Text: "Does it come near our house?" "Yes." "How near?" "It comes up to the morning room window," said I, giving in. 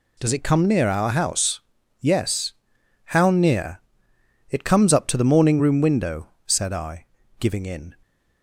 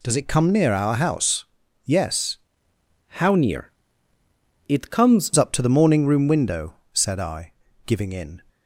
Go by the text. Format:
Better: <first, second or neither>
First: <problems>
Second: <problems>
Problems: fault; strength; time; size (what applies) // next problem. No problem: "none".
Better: first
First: none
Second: changes voice from "How" to "comes"; from 3.1 to 5.3 s; 2.2 s long